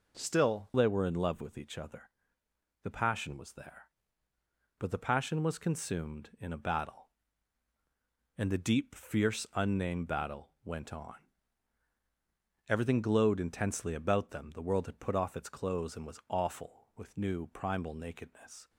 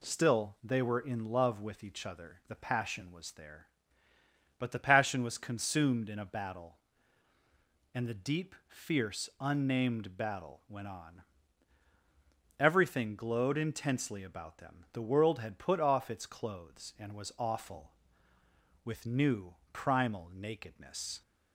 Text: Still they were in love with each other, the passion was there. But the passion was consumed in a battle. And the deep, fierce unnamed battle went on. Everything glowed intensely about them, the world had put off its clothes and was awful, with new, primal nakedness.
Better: second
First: changes voice at "they"; from 0.7 s on; 17.9 s long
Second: none

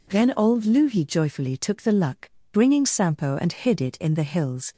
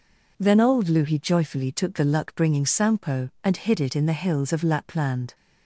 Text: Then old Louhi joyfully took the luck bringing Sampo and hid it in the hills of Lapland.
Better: second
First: pauses between "luck" and "bringing"; slight; at 2.3 s; 0.20 s long // stops before "of Lapland"; at 4.7 s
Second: none

